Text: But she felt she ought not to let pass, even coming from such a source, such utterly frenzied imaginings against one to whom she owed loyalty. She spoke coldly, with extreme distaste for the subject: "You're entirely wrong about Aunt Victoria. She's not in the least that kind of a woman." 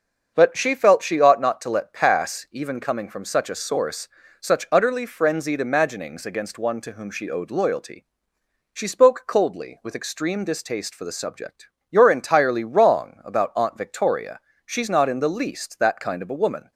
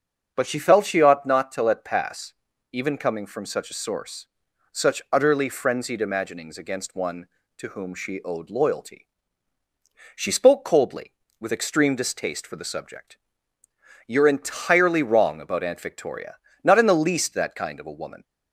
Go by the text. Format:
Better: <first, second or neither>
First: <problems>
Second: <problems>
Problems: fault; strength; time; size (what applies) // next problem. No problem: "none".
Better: first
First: starts louder than the rest; until 1.3 s; 6.5 dB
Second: starts louder than the rest; until 1.3 s; 7 dB // skips "She's"; at 16.5 s